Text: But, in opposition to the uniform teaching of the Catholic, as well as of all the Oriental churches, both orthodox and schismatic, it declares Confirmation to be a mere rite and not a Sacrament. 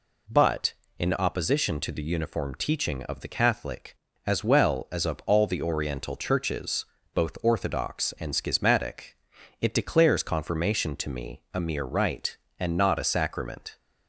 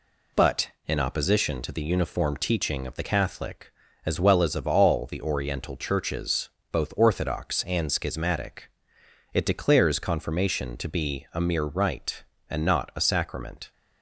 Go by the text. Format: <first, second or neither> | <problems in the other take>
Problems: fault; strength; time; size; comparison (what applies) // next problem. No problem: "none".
second | says "me" for "be"; at 11.0 s